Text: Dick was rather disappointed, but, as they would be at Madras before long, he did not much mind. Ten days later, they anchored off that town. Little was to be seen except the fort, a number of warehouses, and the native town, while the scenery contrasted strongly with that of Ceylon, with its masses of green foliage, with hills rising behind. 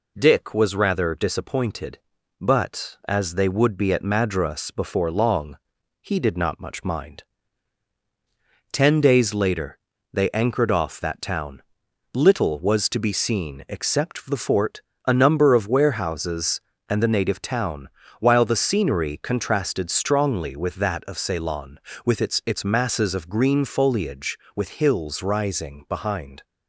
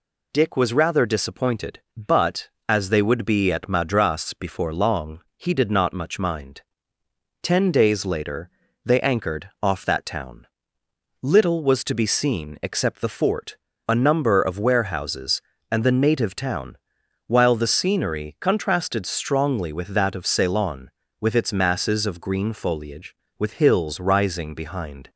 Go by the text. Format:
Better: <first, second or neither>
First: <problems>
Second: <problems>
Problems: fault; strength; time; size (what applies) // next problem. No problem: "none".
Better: second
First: says "its" twice; at 22.4 s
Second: none